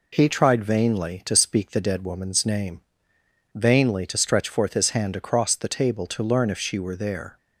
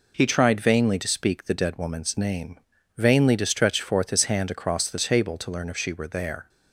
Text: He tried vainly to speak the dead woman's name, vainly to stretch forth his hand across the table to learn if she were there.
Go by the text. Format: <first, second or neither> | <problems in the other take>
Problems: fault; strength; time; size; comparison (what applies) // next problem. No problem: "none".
neither | none